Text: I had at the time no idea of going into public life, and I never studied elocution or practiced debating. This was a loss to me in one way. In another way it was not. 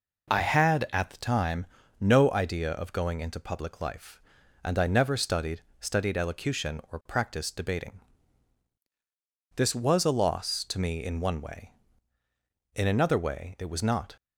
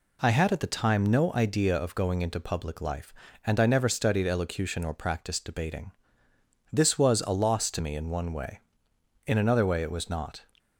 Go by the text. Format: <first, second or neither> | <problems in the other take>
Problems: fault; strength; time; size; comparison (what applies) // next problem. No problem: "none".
second | pauses between "time" and "no"; slight; at 1.6 s; 0.34 s long // says "studied" twice; at 5.8 s